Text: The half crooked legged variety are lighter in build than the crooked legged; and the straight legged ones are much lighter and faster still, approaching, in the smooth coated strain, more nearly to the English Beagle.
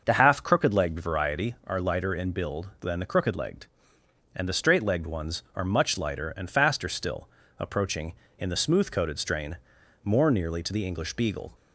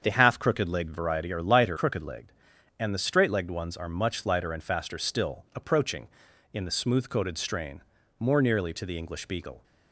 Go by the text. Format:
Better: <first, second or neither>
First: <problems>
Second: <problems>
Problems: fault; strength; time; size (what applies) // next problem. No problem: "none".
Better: first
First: starts louder than the rest; until 1.0 s; 6.5 dB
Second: starts louder than the rest; until 1.0 s; 7 dB // skips "in build than the"; at 1.7 s